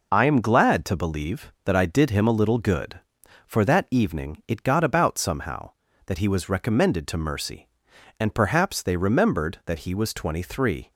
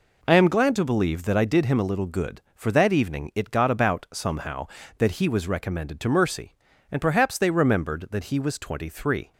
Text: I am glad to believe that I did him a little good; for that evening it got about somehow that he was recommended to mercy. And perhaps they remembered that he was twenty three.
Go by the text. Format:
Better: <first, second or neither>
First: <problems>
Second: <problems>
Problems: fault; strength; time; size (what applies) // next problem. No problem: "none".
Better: neither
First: none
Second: none